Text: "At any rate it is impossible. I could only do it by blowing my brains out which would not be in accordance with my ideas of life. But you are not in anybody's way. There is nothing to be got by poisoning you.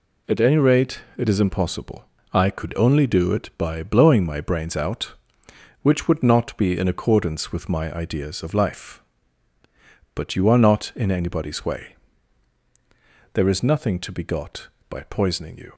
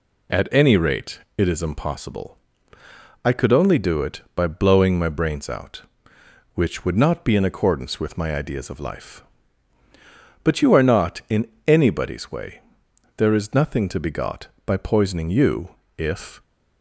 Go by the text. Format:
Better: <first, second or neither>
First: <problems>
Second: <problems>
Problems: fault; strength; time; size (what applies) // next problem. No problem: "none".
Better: first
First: pauses between "rate" and "it"; slight; at 1.0 s; 0.18 s long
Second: pauses between "rate" and "it"; slight; at 1.1 s; 0.18 s long // pauses between "in" and "anybody's"; slight; at 11.4 s; 0.18 s long // goes on to say "If"; slight; from 15.9 s on; 0.46 s long